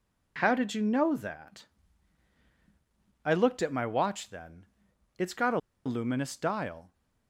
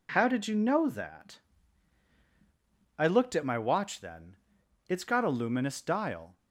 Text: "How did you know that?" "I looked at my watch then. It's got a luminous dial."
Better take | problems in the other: second | pauses between "a" and "luminous"; slight; at 5.5 s; 0.26 s long

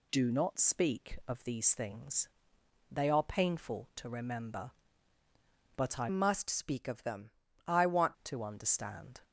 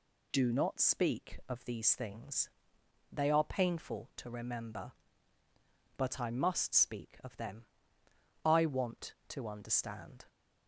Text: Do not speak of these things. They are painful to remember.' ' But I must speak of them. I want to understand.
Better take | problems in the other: second | changes voice from "must" to "want"; from 6.0 to 8.1 s; 2.1 s long

